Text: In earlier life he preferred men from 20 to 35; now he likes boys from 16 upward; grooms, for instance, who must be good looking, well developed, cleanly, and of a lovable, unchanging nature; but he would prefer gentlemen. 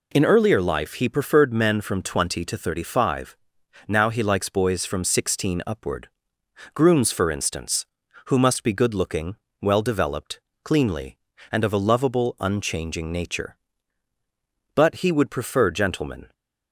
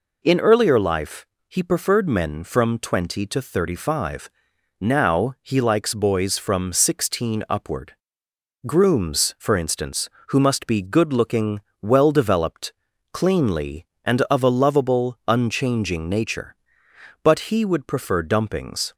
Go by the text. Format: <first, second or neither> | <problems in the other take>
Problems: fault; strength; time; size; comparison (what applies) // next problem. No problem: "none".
first | pauses between "life" and "he"; slight; at 1.2 s; 0.22 s long // says "dumpings" for "gentlemen"; at 18.2 s